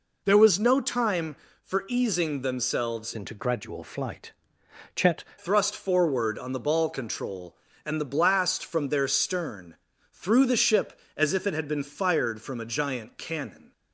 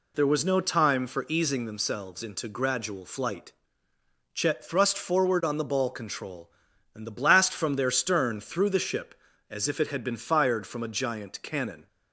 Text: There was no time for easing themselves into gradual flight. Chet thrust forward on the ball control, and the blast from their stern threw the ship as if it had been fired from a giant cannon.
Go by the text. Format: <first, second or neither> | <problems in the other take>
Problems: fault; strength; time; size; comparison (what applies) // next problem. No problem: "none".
second | changes voice from "into" to "Chet"; from 3.1 to 5.2 s; 2.1 s long // pauses between "stern" and "threw"; at 9.7 s; 0.38 s long